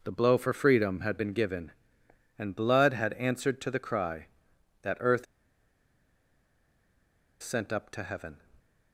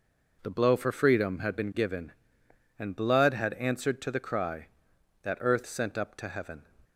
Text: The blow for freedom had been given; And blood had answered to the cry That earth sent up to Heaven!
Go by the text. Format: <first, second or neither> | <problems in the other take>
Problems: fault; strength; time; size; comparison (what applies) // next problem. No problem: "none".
second | pauses between "earth" and "sent"; strong; at 5.2 s; 2.1 s long